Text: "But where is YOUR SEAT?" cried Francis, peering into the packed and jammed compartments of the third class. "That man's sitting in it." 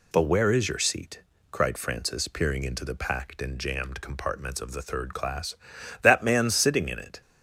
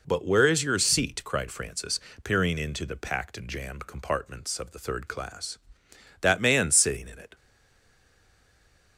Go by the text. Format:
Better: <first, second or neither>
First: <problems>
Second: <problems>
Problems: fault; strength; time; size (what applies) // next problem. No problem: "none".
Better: first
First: none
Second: stays silent after the last word; noticeable; from 7.3 s on; 1.6 s long